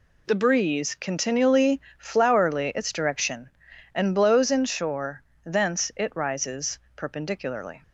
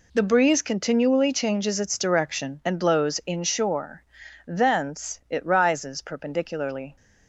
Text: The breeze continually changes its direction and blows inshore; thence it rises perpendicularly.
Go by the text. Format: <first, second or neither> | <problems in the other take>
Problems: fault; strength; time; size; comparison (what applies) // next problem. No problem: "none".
second | says "flowerly" for "changes"; at 2.0 s // pauses between "rises" and "perpendicularly"; slight; at 6.8 s; 0.16 s long